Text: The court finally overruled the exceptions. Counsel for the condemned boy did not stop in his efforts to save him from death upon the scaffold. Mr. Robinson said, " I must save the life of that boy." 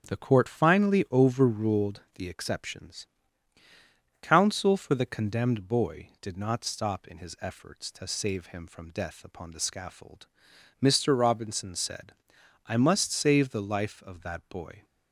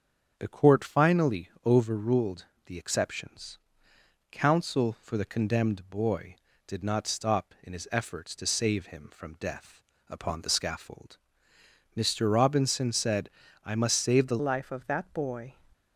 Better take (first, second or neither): first